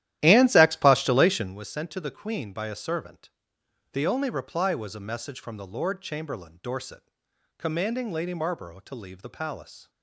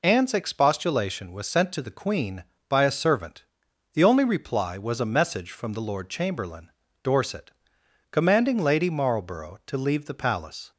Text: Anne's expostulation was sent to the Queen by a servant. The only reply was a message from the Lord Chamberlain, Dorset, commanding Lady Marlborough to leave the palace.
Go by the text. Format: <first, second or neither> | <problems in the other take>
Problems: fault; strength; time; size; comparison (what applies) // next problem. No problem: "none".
second | starts louder than the rest; strong; until 1.6 s; 13 dB